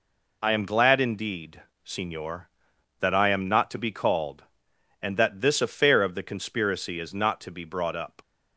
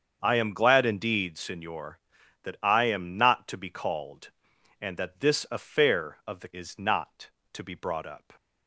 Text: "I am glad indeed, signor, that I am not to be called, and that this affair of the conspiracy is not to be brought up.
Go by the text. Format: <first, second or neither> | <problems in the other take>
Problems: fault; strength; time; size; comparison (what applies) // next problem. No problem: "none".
first | starts louder than the rest; strong; until 1.2 s; 7 dB // skips "conspiracy"; at 6.5 s